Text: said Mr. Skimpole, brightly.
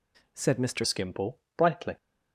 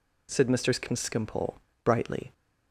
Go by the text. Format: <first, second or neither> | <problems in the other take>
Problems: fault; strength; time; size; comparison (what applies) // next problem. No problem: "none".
second | changes voice at "Skimpole"; from 0.8 s on; 1.1 s long